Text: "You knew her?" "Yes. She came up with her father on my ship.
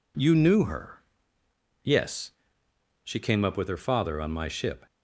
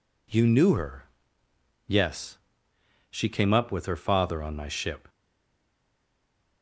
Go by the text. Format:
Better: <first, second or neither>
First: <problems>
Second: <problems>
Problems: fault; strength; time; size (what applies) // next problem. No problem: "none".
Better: first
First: none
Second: stays silent after the last word; noticeable; from 5.0 s on; 1.6 s long